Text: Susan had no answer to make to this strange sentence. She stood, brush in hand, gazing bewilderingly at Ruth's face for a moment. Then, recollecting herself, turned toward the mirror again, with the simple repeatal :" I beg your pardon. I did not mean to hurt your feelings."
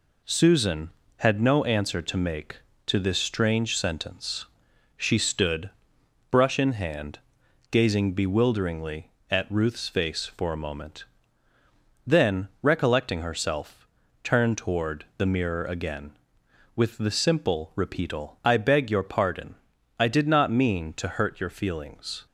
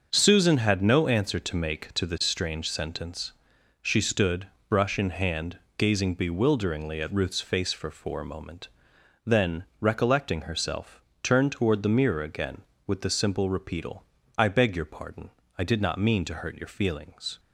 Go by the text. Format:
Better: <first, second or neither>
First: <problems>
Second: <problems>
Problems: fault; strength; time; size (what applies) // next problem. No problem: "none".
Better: first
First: none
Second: starts louder than the rest; until 1.1 s; 6.5 dB // says "for" twice; at 7.8 s